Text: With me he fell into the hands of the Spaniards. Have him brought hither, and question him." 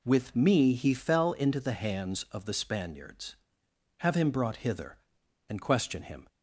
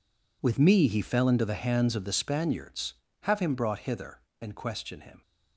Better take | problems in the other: first | gets quieter; strong; throughout; 15.5 dB

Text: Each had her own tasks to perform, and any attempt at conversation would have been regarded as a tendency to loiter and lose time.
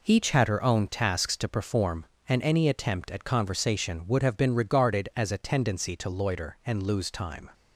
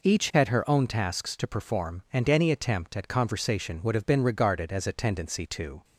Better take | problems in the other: first | stops before "loiter and lose time"; at 5.8 s

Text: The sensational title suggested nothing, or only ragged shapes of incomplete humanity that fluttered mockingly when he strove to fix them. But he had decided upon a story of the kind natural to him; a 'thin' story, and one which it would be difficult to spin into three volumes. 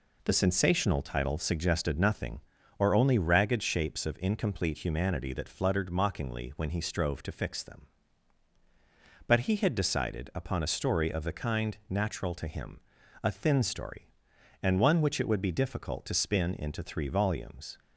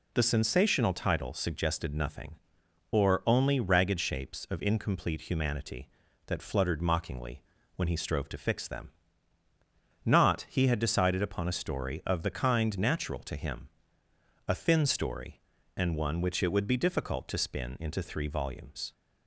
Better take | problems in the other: first | pauses between "mockingly" and "when"; slight; at 7.4 s; 0.34 s long // says "Not" for "But"; at 10.0 s

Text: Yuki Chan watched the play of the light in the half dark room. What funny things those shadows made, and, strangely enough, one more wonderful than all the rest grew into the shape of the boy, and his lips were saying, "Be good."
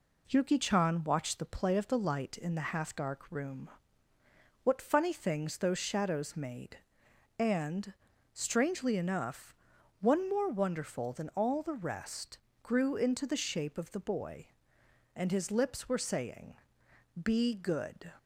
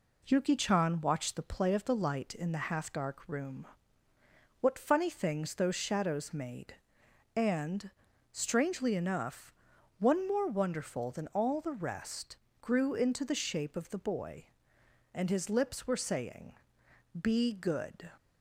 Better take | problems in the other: neither | pauses between "rest" and "grew"; slight; the same in both

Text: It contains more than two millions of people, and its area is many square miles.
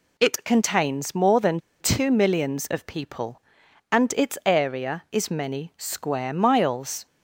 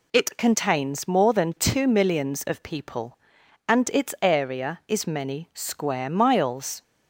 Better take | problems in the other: second | pauses between "than" and "two"; slight; at 1.5 s; 0.21 s long

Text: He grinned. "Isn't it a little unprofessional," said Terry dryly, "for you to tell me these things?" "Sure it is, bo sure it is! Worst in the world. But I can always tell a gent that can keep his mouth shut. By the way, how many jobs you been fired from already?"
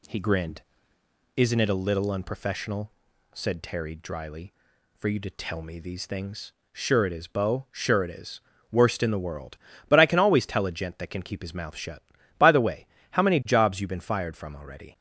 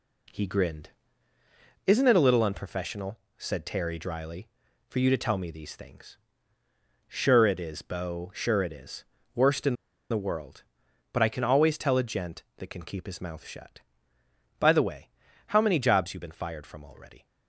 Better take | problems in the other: first | pauses between "in" and "the"; slight; at 9.7 s; 0.35 s long

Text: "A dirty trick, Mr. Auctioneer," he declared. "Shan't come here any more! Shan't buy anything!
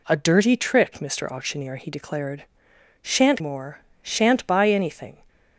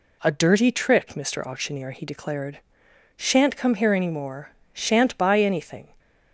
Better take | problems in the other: second | skips "come here any"; at 3.4 s

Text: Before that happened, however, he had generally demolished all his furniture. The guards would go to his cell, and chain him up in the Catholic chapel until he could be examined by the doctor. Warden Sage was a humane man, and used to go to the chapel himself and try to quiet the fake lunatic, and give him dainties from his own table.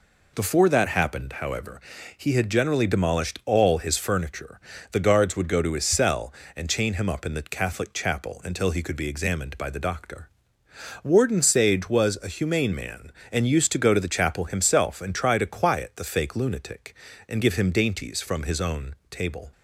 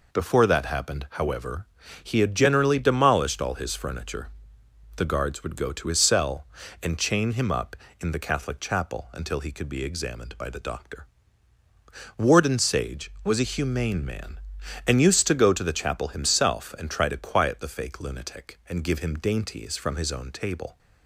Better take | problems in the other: neither | none

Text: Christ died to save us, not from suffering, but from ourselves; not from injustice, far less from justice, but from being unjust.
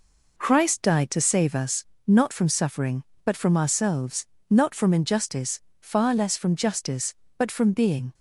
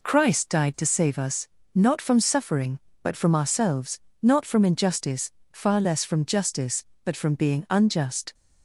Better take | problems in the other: second | stops before "unjust"; at 8.1 s

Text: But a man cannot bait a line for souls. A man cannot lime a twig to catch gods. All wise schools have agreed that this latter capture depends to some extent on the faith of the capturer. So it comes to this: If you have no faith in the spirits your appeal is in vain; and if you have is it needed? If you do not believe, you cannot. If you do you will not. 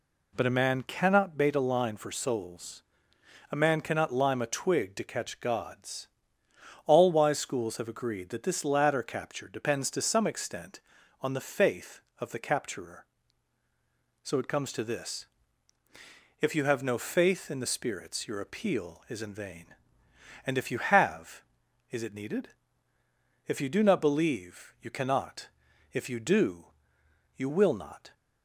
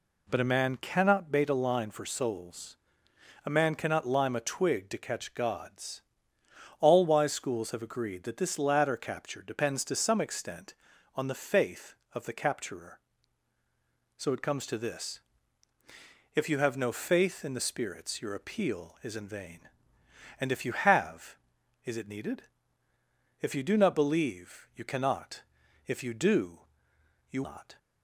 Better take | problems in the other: first | pauses between "do" and "you"; noticeable; at 26.5 s; 0.70 s long; noticeable in the first // skips "will"; at 27.4 s

